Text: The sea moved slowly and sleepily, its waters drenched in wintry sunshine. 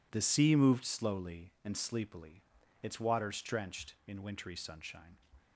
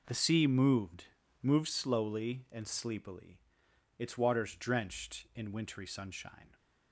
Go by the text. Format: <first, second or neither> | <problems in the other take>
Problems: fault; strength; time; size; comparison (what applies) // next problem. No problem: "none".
first | says "moved" twice; at 1.4 s